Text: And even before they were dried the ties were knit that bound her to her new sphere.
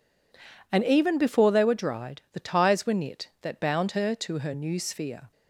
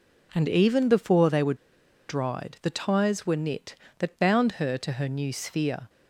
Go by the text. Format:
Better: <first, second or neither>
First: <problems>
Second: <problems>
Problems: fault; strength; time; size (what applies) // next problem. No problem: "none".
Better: first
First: none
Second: pauses between "were" and "dried"; noticeable; at 1.5 s; 0.53 s long